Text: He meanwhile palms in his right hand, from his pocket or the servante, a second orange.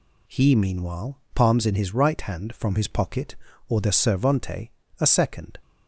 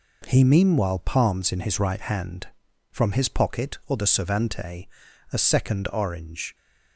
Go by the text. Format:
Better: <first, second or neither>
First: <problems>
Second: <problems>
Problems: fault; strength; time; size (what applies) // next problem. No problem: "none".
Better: second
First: stops before "orange"; at 5.6 s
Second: none